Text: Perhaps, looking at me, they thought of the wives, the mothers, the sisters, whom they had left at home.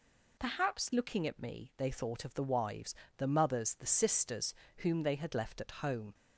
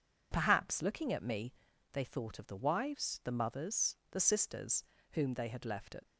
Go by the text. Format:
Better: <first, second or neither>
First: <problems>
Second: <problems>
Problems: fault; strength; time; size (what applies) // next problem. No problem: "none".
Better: first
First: none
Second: stops before "home"; at 6.0 s